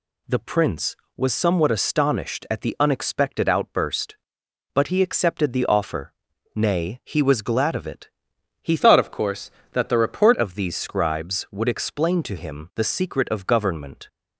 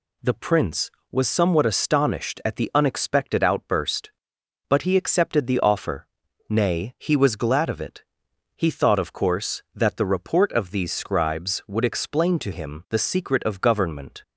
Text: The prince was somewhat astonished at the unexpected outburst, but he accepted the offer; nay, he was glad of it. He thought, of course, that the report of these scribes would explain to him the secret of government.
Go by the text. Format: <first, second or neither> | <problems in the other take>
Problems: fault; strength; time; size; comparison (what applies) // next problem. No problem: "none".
second | changes voice from "thought" to "report"; from 8.7 to 10.3 s; 1.6 s long